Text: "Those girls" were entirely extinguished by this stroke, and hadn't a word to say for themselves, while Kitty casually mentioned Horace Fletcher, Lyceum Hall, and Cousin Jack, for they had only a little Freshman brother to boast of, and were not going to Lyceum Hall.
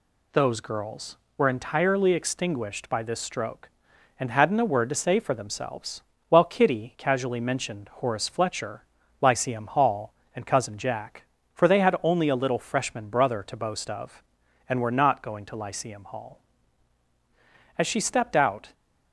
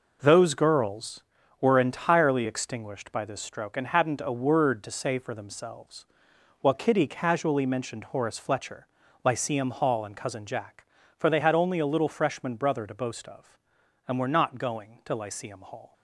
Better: second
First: goes on to say "As she stepped out"; noticeable; from 17.7 s on; 0.96 s long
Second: none

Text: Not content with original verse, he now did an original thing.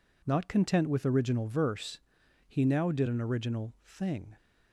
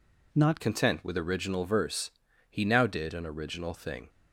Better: first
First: none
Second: changes voice at "content"; from 0.6 s on; 3.4 s long

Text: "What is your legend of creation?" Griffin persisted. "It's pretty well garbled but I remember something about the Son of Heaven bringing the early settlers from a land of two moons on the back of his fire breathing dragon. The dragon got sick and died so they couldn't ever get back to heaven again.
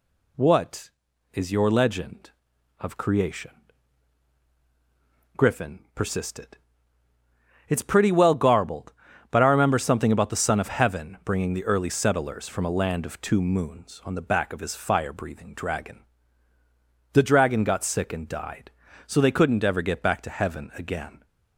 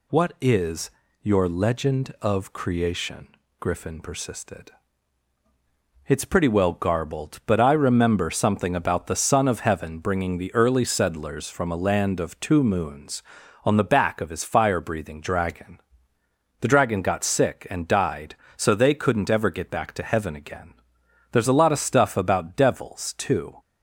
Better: first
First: none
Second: pauses between "is" and "your"; slight; at 0.8 s; 0.32 s long // goes on to say "There's a lot of stuff about devils too"; strong; from 21.3 s on; 2.2 s long

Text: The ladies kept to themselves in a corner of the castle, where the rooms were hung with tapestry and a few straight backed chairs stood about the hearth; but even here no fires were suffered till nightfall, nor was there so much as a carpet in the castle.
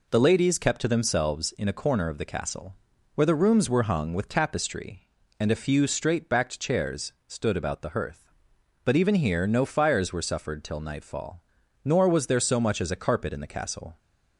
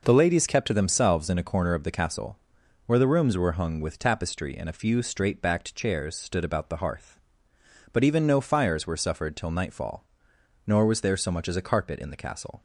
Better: first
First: none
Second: skips "here"; at 8.2 s

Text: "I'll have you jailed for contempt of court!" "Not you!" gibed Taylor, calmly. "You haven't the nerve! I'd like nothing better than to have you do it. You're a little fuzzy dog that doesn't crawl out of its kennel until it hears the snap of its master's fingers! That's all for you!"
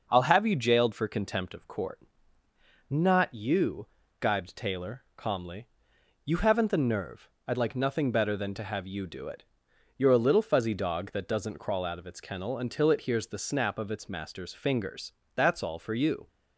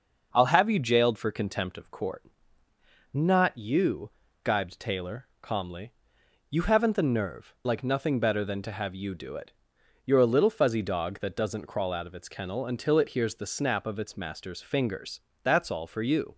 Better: first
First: none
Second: skips "I'd"; at 7.5 s

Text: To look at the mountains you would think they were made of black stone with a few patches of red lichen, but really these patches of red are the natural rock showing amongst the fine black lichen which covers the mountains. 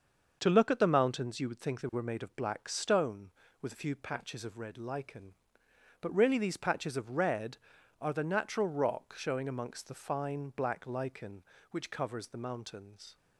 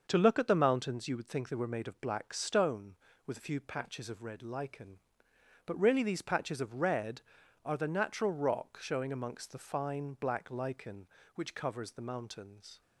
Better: neither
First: starts louder than the rest; until 1.4 s; 6.5 dB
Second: starts louder than the rest; until 1.1 s; 6.5 dB

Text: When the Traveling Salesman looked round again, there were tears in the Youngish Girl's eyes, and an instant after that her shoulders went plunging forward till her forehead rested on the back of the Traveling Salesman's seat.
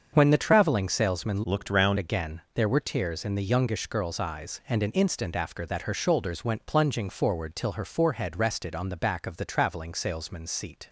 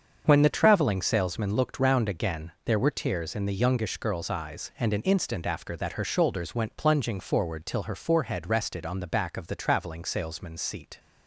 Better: second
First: starts louder than the rest; strong; until 1.1 s; 7 dB // changes voice from "looked" to "round"; from 1.4 to 1.9 s; 0.5 s long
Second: starts louder than the rest; strong; until 1.2 s; 7 dB

